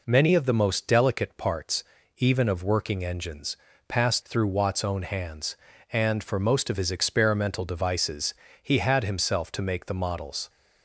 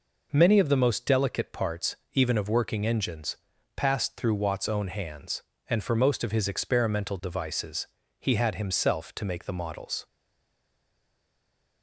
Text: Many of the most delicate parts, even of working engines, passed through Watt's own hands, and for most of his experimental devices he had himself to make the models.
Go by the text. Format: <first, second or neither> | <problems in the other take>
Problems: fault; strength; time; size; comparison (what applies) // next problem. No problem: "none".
first | pauses between "devices" and "he"; slight; at 7.8 s; 0.32 s long; slight in the first // stays silent after the last word; noticeable; from 10.0 s on; 1.8 s long